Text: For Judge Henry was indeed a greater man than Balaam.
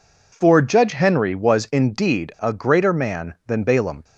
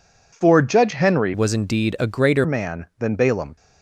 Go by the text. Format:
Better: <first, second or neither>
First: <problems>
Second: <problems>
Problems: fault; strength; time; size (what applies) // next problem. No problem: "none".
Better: first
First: none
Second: changes voice from "was" to "greater"; from 1.3 to 2.4 s; 1.1 s long